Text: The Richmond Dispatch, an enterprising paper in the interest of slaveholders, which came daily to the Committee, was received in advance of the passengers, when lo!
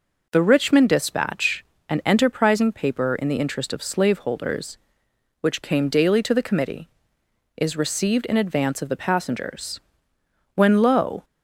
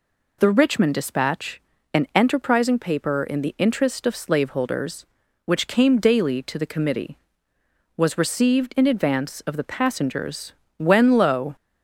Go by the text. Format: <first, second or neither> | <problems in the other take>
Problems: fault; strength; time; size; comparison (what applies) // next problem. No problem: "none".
second | says "is" for "was"; at 7.5 s